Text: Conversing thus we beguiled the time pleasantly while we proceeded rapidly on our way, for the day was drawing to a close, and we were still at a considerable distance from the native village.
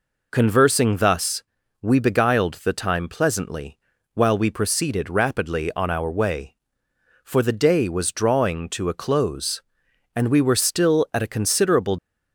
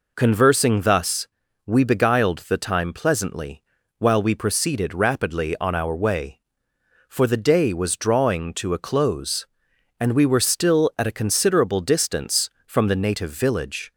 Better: second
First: pauses between "thus" and "we"; at 1.4 s; 0.40 s long // pauses between "pleasantly" and "while"; slight; at 3.7 s; 0.36 s long // stops before "distance from the native village"; at 11.9 s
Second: pauses between "thus" and "we"; at 1.2 s; 0.40 s long // pauses between "pleasantly" and "while"; slight; at 3.6 s; 0.36 s long

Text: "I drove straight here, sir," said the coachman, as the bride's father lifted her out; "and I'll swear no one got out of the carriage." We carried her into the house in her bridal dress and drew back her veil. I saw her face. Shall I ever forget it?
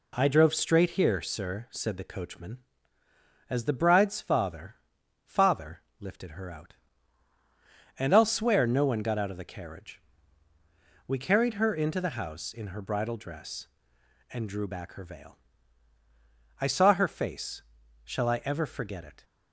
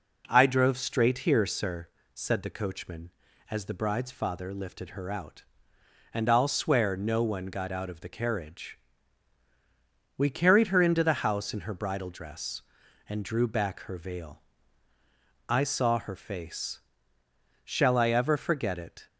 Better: second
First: says "father" twice; at 5.2 s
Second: none

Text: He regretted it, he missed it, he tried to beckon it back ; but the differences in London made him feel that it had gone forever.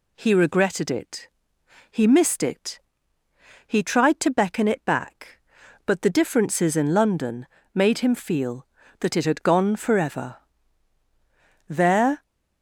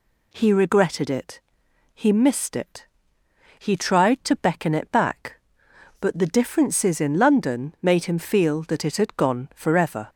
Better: second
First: pauses between "London" and "made"; slight; at 7.4 s; 0.28 s long // goes on to say "There"; from 11.6 s on; 0.54 s long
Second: none

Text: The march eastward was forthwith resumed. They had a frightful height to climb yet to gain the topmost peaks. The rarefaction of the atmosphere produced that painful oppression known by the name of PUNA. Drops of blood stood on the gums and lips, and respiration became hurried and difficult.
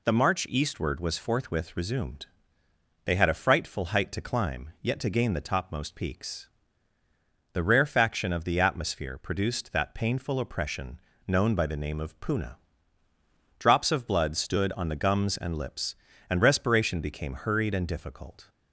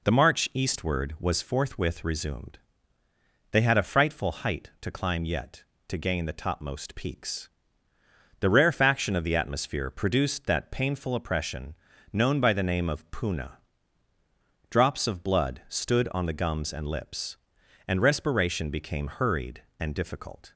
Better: neither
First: pauses between "oppression" and "known"; slight; at 10.9 s; 0.26 s long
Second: pauses between "oppression" and "known"; slight; at 11.7 s; 0.36 s long

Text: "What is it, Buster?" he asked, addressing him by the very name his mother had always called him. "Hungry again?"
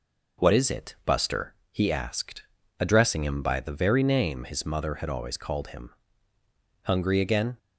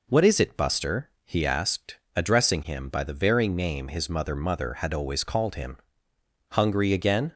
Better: first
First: none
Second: says "mother" twice; at 4.3 s

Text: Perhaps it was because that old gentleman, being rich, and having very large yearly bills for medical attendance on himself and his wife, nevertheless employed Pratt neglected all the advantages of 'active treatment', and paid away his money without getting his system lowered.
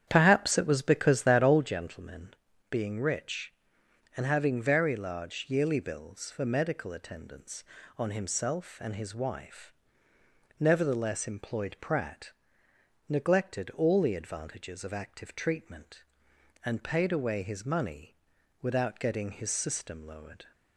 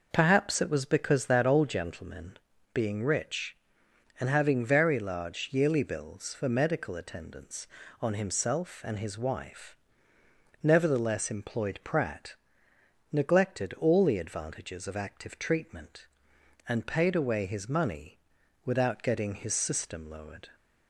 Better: second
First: starts louder than the rest; strong; until 1.6 s; 9 dB // pauses between "Pratt" and "neglected"; noticeable; at 12.3 s; 0.78 s long // pauses between "money" and "without"; noticeable; at 18.1 s; 0.46 s long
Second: pauses between "Pratt" and "neglected"; noticeable; at 12.3 s; 0.78 s long // pauses between "money" and "without"; noticeable; at 18.1 s; 0.46 s long

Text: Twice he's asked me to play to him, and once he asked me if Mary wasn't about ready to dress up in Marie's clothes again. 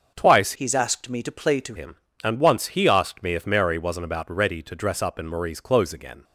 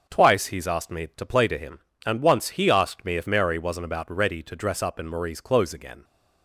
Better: second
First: starts louder than the rest; until 1.1 s; 6.5 dB // changes voice from "he's" to "to"; from 0.5 to 1.7 s; 1.2 s long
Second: starts louder than the rest; until 1.1 s; 7 dB

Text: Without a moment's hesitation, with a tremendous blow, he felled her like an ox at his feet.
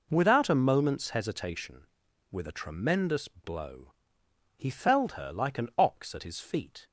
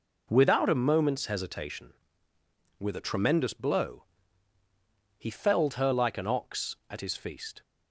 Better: first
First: none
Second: says "feast" for "feet"; at 7.1 s

